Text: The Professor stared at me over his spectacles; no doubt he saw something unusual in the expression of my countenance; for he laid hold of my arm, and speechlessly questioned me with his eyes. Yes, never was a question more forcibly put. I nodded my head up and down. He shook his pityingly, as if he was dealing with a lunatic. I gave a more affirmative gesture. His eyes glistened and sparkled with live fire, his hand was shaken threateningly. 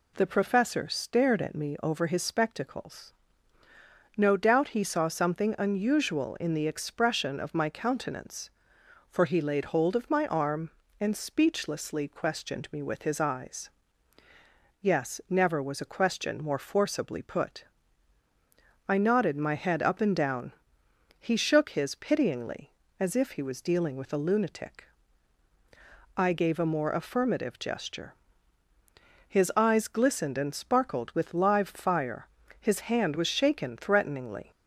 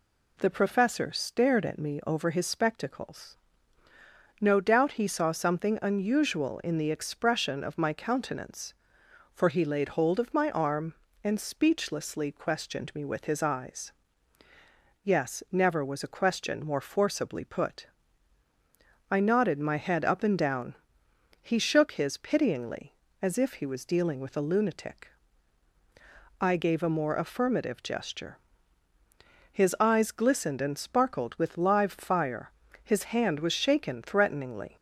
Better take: neither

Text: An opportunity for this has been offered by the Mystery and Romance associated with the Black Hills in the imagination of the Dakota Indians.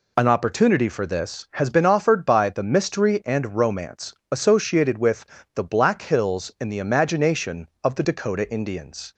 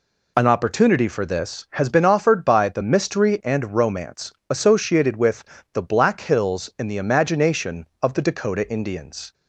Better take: neither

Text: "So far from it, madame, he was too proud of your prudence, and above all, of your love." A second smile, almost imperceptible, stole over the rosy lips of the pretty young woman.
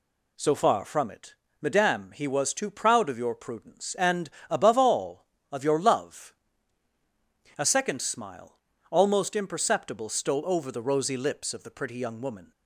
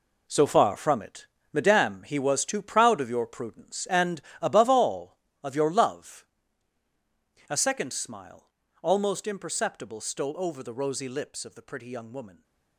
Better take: first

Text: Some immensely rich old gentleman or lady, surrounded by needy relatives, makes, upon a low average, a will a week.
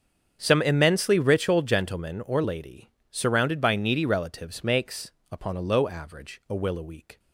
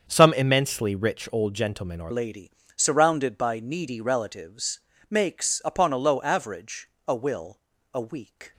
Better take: first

